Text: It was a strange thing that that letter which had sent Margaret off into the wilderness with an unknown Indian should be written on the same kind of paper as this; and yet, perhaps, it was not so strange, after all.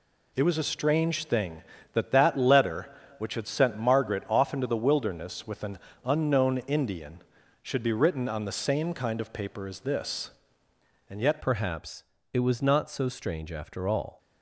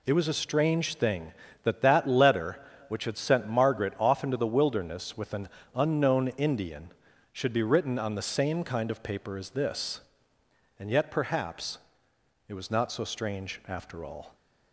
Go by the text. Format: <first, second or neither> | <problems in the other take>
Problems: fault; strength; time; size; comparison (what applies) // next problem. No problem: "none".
second | pauses between "an" and "unknown"; slight; at 5.7 s; 0.28 s long; slight in the second // changes voice at "perhaps"; from 11.4 s on; 2.4 s long